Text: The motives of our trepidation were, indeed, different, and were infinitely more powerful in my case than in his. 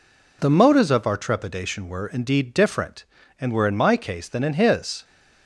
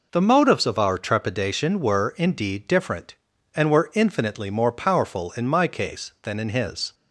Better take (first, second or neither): second